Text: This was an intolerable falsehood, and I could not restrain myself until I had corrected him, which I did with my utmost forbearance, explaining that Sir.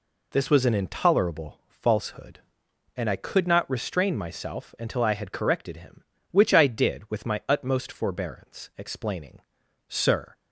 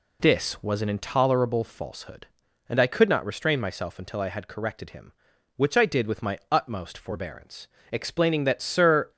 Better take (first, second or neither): second